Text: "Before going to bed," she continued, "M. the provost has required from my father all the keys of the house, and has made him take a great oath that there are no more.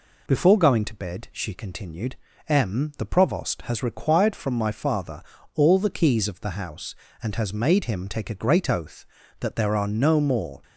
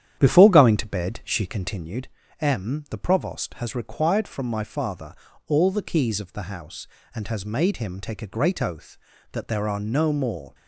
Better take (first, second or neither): first